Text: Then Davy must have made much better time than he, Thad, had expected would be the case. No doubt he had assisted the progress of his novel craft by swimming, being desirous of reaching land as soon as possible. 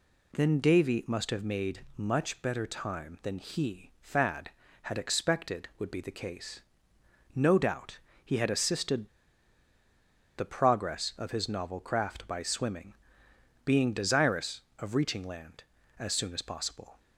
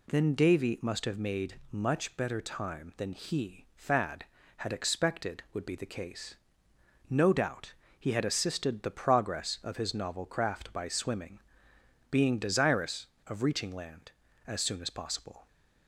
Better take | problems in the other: second | pauses between "doubt" and "he"; slight; at 7.9 s; 0.26 s long; slight in the second // pauses between "assisted" and "the"; strong; at 9.0 s; 1.3 s long

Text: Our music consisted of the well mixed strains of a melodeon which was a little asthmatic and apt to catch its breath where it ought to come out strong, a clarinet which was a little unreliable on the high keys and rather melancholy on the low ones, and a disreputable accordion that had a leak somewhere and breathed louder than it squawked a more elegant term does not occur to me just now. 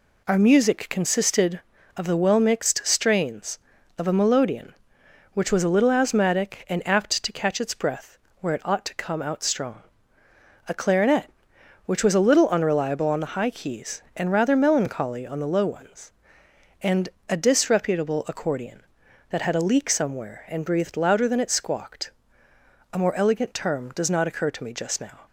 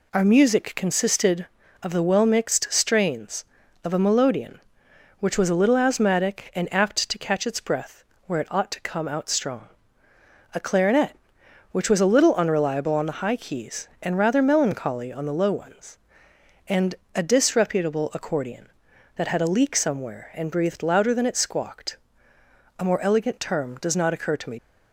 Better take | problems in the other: first | pauses between "breath" and "where"; slight; at 8.0 s; 0.22 s long; slight in the first // pauses between "and" and "a"; slight; at 16.9 s; 0.18 s long; slight in the first // pauses between "squawked" and "a"; noticeable; at 21.9 s; 0.82 s long; noticeable in the first // stops before "just now"; at 24.5 s

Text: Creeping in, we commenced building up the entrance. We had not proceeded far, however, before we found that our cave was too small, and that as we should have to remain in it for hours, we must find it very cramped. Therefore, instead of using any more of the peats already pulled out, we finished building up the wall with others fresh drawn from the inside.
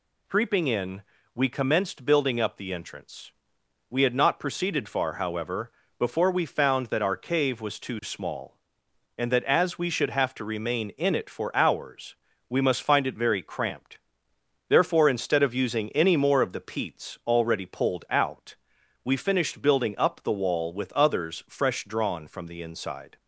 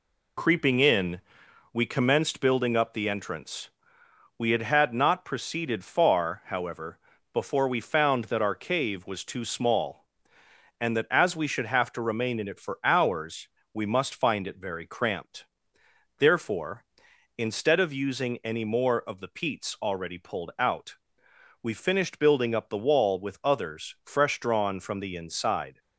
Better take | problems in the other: first | says "had" twice; at 4.6 s

